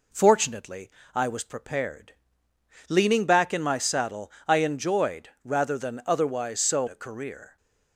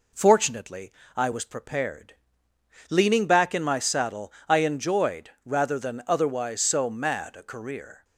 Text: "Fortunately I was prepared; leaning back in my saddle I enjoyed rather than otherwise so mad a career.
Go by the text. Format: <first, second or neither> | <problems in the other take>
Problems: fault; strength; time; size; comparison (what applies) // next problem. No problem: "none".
second | pauses between "Fortunately" and "I"; slight; at 0.9 s; 0.24 s long; slight in the second // pauses between "saddle" and "I"; slight; at 4.2 s; 0.16 s long; slight in the second // pauses between "enjoyed" and "rather"; slight; at 5.2 s; 0.16 s long; slight in the second // skips "mad"; at 6.8 s